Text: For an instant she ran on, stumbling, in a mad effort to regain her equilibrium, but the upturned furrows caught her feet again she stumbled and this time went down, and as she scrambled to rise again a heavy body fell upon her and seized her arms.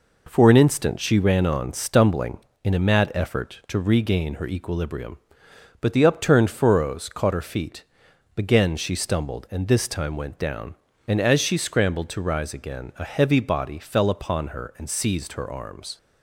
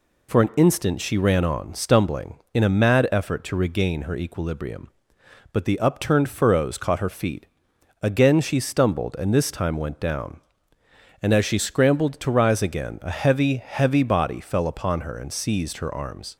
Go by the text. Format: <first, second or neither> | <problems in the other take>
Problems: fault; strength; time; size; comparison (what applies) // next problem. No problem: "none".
first | pauses between "feet" and "again"; noticeable; at 7.4 s; 0.56 s long; noticeable in the first // says "heavy" twice; at 13.5 s